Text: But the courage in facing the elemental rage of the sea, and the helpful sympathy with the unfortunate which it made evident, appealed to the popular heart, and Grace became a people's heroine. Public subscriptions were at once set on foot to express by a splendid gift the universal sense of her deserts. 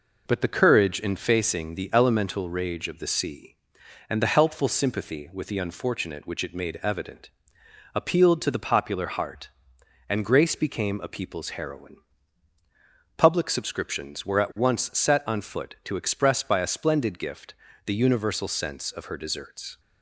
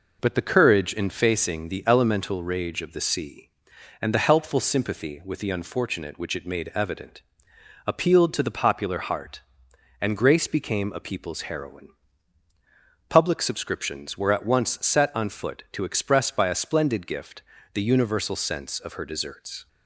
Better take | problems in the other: neither | pauses between "gift" and "the"; slight; the same in both

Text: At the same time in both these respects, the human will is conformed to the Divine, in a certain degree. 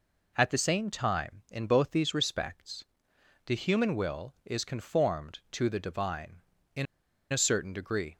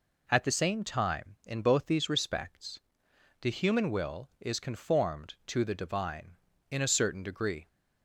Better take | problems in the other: second | pauses between "in" and "a"; noticeable; at 6.8 s; 0.47 s long

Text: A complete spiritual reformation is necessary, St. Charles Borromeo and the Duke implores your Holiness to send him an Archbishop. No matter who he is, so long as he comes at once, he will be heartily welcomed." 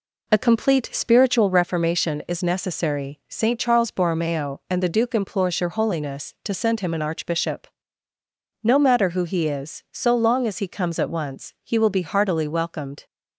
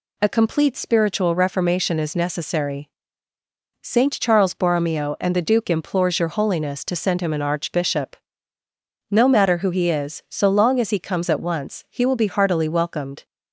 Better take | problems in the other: second | starts louder than the rest; slight; until 1.7 s; 3 dB

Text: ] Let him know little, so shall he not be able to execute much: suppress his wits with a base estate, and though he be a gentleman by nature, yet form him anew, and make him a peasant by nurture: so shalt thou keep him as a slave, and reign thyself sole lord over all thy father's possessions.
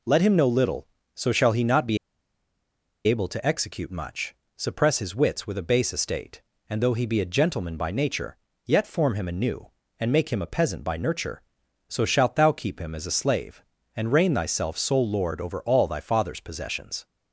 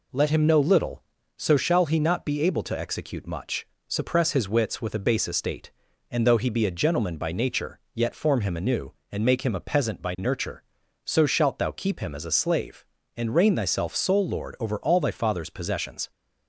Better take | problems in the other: second | pauses between "be" and "able"; at 1.9 s; 1.0 s long

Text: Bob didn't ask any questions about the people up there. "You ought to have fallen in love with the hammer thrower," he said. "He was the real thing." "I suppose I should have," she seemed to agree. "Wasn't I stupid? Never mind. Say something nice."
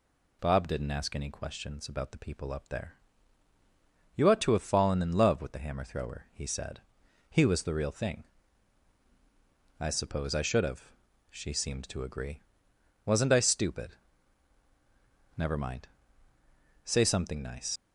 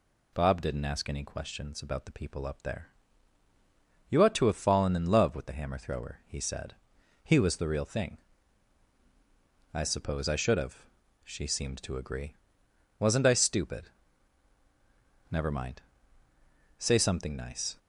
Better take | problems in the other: second | leaves "nice" unfinished; at 17.7 s; 80 ms

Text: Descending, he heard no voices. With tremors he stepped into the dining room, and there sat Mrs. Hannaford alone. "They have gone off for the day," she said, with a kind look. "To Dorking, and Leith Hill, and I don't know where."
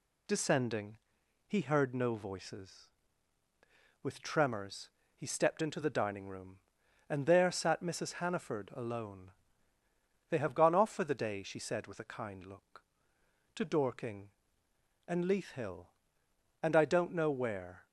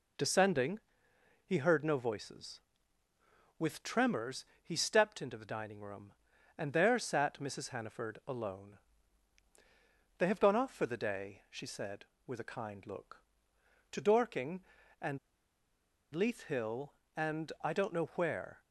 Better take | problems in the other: first | pauses between "tremors" and "he"; slight; at 4.4 s; 0.18 s long; slight in the first // pauses between "and" and "Leith"; noticeable; at 15.1 s; 0.96 s long

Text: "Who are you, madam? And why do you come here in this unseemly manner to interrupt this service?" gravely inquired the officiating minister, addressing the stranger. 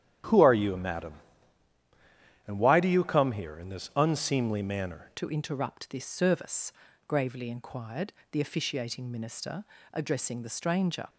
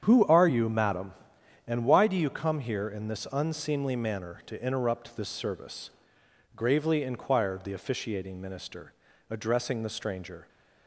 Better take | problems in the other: second | starts louder than the rest; strong; until 2.5 s; 10 dB; strong in the second // changes voice at "to"; from 5.1 s on; 5.9 s long // pauses between "inquired" and "the"; slight; at 8.1 s; 0.18 s long

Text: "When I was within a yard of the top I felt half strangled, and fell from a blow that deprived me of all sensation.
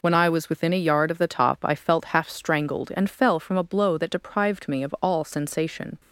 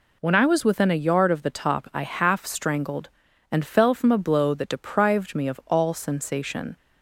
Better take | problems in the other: first | skips "felt"; at 2.0 s

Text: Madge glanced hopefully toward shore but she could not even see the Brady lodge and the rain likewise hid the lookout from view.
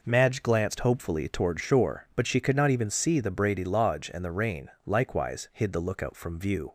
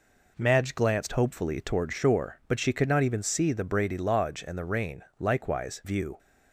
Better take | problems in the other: first | pauses between "rain" and "likewise"; slight; at 5.0 s; 0.16 s long; slight in the first // skips "hid the lookout from"; at 5.8 s

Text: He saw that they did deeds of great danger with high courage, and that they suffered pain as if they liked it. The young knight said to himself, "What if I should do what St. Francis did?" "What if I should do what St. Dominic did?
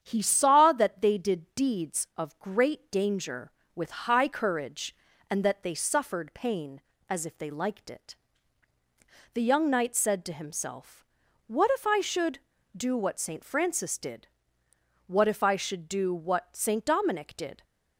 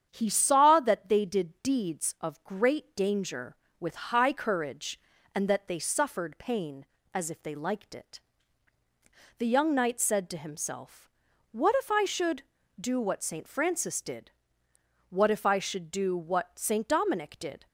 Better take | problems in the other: neither | starts louder than the rest; strong; the same in both

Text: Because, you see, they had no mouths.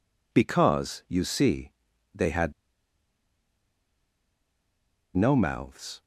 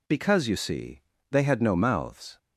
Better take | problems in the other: second | pauses between "had" and "no"; strong; at 2.5 s; 2.6 s long

